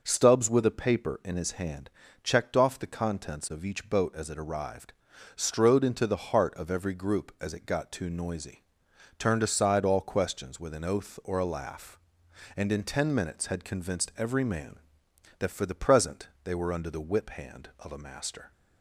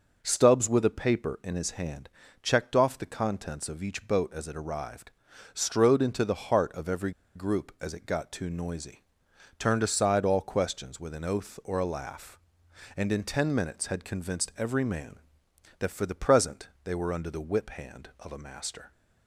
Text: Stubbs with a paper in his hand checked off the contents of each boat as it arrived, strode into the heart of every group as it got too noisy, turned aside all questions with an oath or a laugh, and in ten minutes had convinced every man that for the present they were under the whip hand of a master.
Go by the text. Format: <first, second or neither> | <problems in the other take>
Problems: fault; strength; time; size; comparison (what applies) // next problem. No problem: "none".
first | pauses between "hand" and "checked"; slight; at 2.0 s; 0.34 s long; slight in the first // pauses between "every" and "group"; slight; at 7.1 s; 0.24 s long // pauses between "present" and "they"; slight; at 16.6 s; 0.16 s long; slight in the first